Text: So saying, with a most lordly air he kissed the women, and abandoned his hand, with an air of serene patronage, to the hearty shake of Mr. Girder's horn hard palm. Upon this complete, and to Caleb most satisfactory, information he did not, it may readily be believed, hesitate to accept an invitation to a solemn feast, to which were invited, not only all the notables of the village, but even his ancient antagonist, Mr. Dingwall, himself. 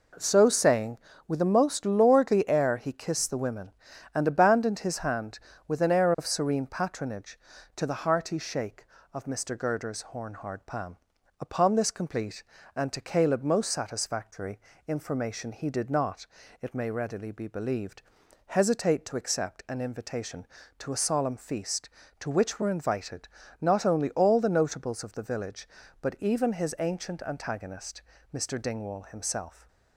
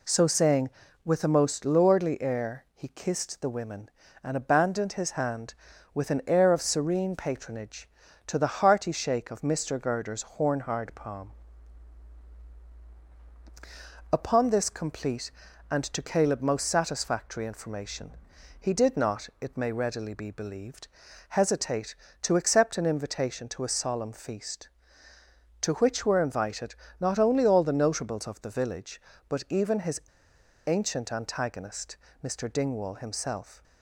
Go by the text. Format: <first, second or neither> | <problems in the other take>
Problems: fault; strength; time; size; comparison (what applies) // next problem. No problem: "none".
first | pauses between "information" and "he"; noticeable; at 18.1 s; 0.48 s long // pauses between "his" and "ancient"; noticeable; at 30.0 s; 0.65 s long